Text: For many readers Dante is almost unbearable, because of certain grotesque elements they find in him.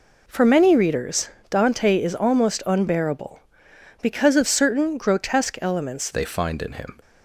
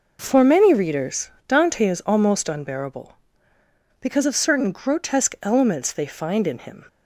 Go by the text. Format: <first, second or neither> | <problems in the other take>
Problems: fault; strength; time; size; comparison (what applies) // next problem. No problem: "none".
second | pauses between "readers" and "Dante"; slight; at 1.2 s; 0.20 s long; slight in the second // changes voice at "they"; from 6.1 s on; 0.8 s long